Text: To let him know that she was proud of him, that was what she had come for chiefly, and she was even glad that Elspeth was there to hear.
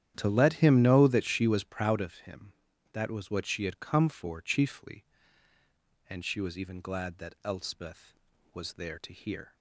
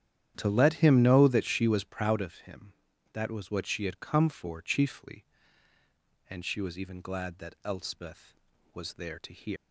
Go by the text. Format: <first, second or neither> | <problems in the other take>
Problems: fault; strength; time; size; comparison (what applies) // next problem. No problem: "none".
first | starts louder than the rest; strong; until 1.3 s; 10.5 dB; strong in the first // leaves "hear" unfinished; at 9.5 s; 195 ms